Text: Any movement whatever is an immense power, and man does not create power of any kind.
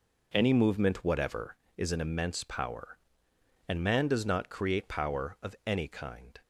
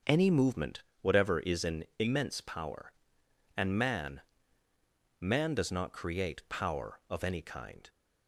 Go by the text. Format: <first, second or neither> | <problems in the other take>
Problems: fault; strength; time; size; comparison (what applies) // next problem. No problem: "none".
first | starts louder than the rest; until 1.2 s; 6.5 dB // pauses between "movement" and "whatever"; slight; at 0.8 s; 0.18 s long // says "man" twice; at 5.2 s